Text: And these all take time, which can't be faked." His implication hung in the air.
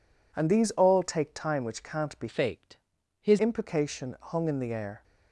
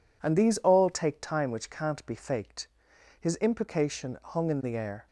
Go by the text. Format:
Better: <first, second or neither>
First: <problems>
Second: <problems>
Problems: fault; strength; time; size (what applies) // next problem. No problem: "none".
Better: second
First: changes voice from "faked" to "His"; from 2.2 to 3.3 s; 1.1 s long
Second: none